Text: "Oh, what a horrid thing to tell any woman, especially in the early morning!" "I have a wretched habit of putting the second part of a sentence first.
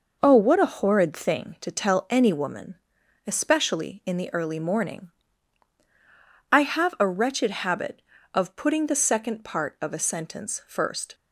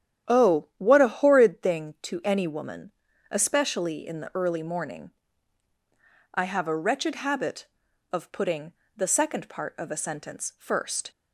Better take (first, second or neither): first